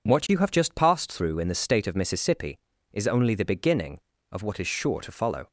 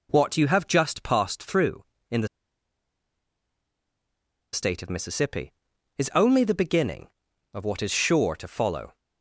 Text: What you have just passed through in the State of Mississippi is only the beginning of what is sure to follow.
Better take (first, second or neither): first